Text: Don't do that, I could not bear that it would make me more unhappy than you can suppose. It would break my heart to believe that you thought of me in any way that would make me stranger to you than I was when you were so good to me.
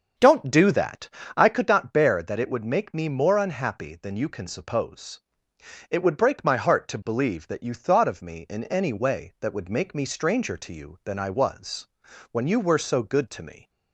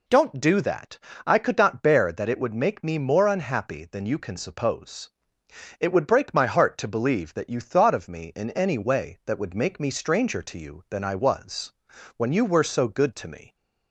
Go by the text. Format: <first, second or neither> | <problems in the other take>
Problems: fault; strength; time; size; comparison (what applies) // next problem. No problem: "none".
second | starts louder than the rest; strong; until 1.7 s; 7 dB // pauses between "was" and "when"; at 11.8 s; 0.44 s long; also in the second